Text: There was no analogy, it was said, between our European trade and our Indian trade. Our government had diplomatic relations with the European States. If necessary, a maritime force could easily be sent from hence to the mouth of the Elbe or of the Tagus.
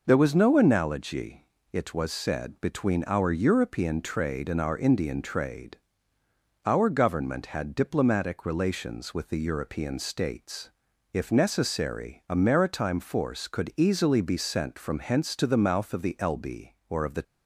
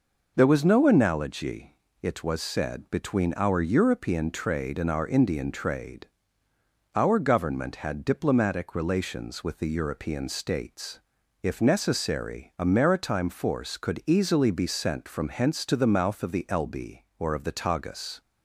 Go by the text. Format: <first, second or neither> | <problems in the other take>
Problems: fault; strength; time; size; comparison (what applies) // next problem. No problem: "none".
second | stops before "Tagus"; at 17.2 s